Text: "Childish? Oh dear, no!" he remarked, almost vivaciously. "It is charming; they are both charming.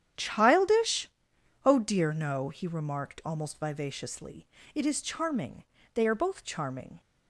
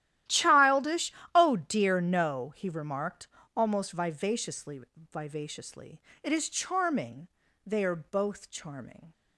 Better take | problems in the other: first | starts louder than the rest; strong; until 1.5 s; 12.5 dB; strong in the first // says "vivaciously" twice; at 5.1 s

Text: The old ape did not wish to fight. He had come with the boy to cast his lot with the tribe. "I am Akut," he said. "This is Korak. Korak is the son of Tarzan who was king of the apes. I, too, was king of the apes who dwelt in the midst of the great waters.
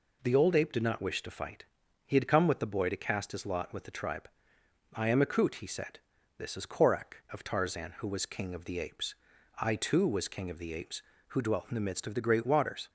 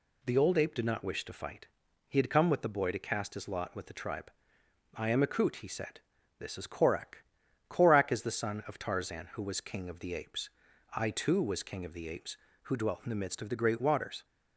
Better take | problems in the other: second | skips "Korak is the son"; at 7.2 s

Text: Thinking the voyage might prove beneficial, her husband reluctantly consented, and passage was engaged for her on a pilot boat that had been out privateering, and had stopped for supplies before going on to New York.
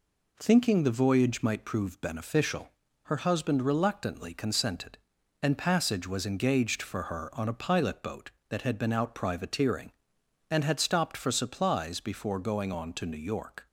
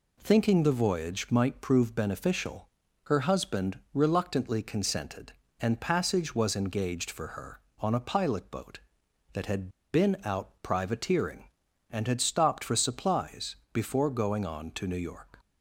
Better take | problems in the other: first | pauses between "had" and "been"; slight; at 9.6 s; 0.23 s long // pauses between "supplies" and "before"; slight; at 13.5 s; 0.18 s long

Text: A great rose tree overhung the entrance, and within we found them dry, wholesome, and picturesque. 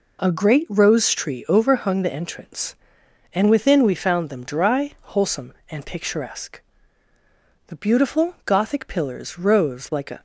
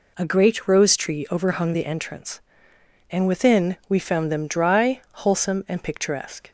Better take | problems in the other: second | goes on to say "The beautiful Gothic pillars rose like a"; strong; from 7.6 s on; 2.5 s long

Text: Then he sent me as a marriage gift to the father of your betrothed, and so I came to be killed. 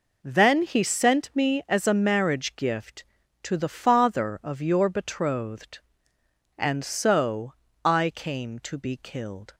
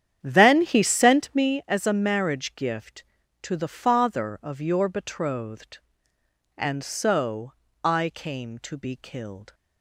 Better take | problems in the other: first | starts louder than the rest; strong; until 1.6 s; 9.5 dB // pauses between "so" and "I"; slight; at 7.5 s; 0.32 s long; slight in the first

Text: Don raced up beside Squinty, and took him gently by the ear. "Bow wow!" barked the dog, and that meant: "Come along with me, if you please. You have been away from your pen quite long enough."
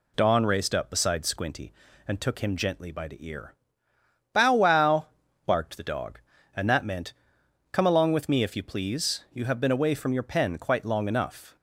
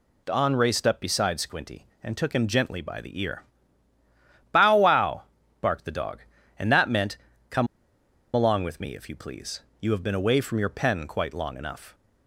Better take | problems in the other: first | pauses between "Come" and "along"; noticeable; at 7.6 s; 0.67 s long

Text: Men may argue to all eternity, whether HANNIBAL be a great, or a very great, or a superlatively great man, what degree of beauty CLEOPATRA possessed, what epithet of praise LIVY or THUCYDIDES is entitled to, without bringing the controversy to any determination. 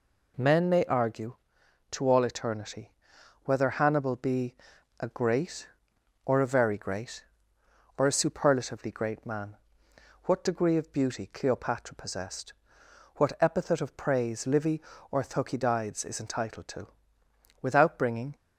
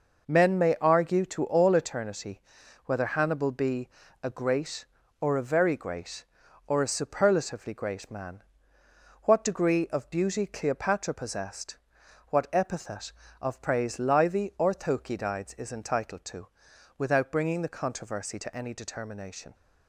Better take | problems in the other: second | pauses between "be" and "a"; at 4.5 s; 0.44 s long; slight in the second // stops before "the controversy to any determination"; at 18.3 s

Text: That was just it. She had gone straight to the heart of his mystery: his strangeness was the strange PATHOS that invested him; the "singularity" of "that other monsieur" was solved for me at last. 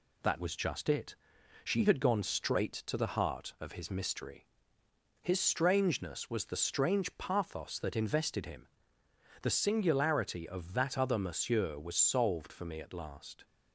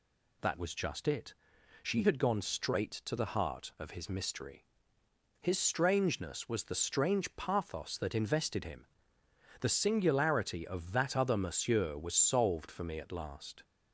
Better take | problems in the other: second | gets quieter; slight; throughout; 2 dB

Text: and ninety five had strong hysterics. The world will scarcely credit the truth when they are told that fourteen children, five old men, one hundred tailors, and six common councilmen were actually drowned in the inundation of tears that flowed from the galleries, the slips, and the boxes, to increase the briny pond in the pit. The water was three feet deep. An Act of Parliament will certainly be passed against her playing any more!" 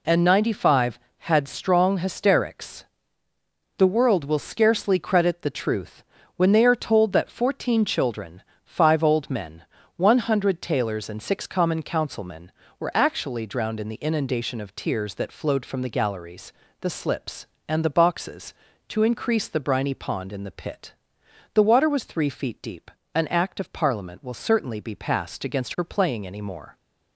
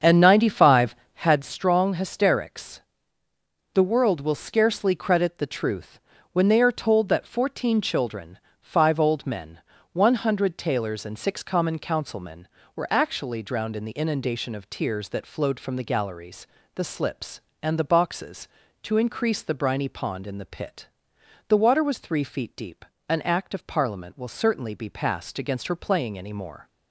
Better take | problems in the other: first | starts louder than the rest; strong; until 1.4 s; 7.5 dB // pauses between "truth" and "when"; slight; at 6.0 s; 0.32 s long; slight in the first

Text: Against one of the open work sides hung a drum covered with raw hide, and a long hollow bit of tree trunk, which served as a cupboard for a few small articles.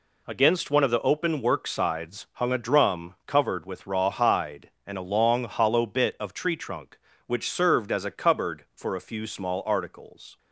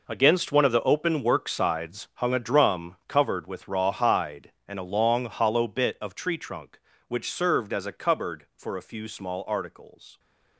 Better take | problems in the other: first | gets quieter; strong; throughout; 12.5 dB

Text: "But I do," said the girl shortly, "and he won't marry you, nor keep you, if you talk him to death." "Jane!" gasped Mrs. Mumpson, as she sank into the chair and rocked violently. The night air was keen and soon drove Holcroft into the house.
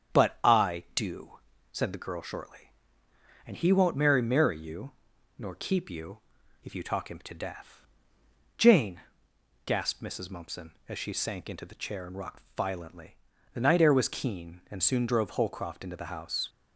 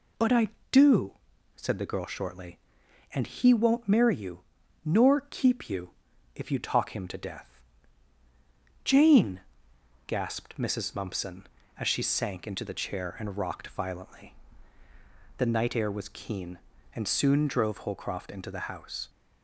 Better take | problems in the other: second | starts louder than the rest; strong; until 1.2 s; 7.5 dB // says "marry" twice; at 4.2 s

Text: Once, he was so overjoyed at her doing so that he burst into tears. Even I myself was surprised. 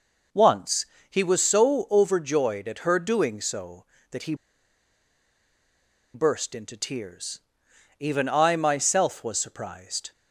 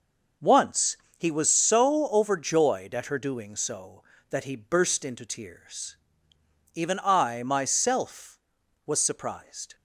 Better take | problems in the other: second | pauses between "he" and "burst"; strong; at 4.3 s; 1.8 s long

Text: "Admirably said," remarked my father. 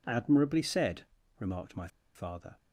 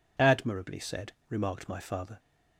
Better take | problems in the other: second | pauses between "my" and "father"; slight; at 1.8 s; 0.27 s long

